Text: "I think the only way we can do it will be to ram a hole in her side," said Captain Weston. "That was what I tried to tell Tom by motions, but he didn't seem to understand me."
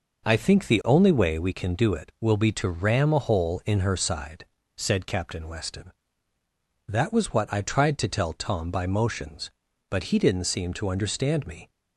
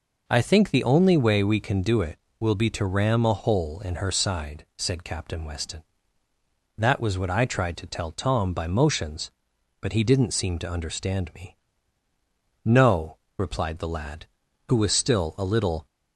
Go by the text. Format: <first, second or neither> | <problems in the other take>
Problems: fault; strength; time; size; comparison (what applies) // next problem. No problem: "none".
first | goes on to say "No replied the lad who was still a little"; strong; from 12.6 s on; 3.2 s long